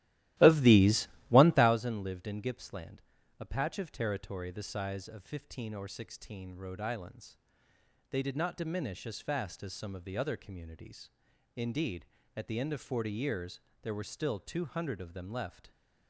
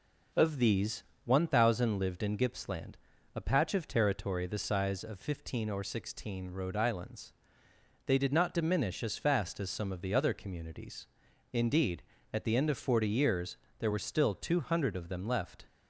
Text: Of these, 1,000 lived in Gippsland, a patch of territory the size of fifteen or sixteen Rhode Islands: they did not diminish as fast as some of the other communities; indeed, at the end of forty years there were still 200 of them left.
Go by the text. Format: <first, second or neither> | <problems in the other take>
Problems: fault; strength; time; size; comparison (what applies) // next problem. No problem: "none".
second | starts louder than the rest; strong; until 1.8 s; 15 dB // pauses between "years" and "there"; slight; at 13.6 s; 0.18 s long; slight in the second